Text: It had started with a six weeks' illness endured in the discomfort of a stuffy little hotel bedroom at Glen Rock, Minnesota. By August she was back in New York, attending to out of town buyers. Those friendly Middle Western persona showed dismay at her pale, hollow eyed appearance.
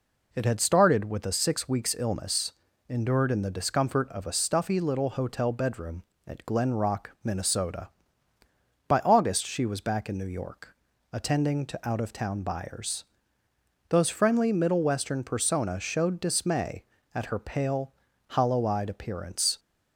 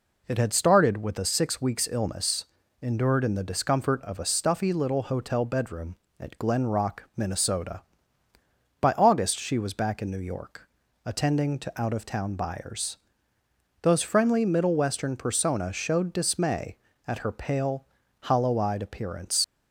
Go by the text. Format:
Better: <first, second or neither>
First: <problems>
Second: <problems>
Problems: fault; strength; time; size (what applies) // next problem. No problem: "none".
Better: first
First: pauses between "illness" and "endured"; slight; at 2.5 s; 0.34 s long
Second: pauses between "illness" and "endured"; slight; at 2.4 s; 0.34 s long // leaves "appearance" unfinished; at 19.4 s; 75 ms